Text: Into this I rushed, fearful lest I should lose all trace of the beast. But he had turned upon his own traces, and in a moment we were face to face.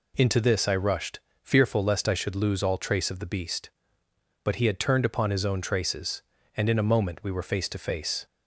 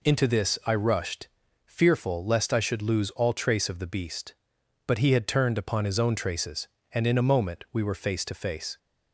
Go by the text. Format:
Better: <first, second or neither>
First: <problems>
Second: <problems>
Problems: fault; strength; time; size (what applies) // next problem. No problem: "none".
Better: neither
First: none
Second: none